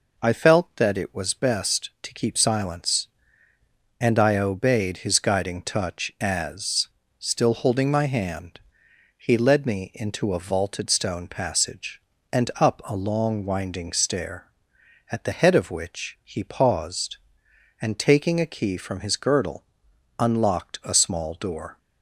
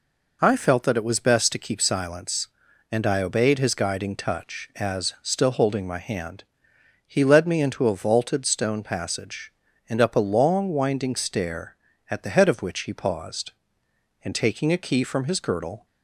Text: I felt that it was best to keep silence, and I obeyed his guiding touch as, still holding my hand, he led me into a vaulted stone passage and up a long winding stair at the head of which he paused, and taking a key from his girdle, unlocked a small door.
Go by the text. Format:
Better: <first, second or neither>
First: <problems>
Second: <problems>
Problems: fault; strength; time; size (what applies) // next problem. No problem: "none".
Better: first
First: none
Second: stops before "unlocked a small door"; at 15.8 s